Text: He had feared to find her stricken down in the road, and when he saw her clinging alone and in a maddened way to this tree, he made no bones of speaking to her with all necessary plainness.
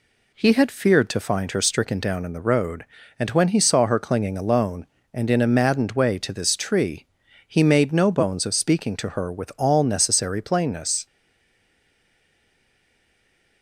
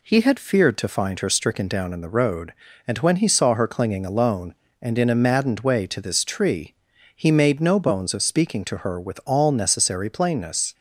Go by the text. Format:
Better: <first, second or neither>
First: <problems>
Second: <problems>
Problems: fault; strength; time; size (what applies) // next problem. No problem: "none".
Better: second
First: stays silent after the last word; strong; from 11.0 s on; 2.6 s long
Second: none